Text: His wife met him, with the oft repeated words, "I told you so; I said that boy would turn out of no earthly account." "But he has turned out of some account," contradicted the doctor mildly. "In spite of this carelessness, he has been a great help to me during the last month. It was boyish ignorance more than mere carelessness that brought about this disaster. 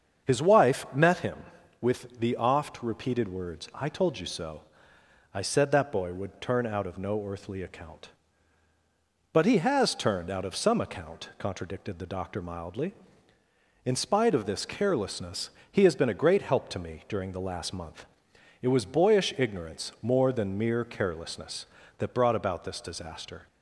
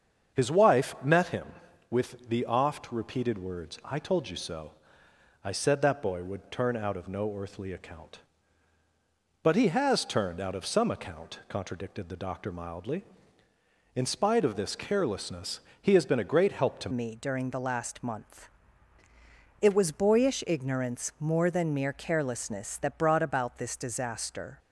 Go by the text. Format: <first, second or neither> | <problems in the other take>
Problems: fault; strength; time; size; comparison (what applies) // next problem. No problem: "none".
first | starts louder than the rest; until 1.4 s; 7 dB; also in the first // changes voice at "me"; from 16.9 s on; 7.6 s long